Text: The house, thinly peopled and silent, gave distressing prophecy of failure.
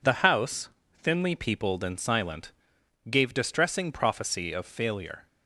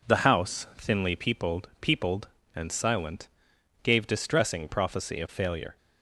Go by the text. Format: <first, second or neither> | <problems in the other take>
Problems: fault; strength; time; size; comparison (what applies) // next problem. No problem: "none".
first | says "peopled" twice; at 1.7 s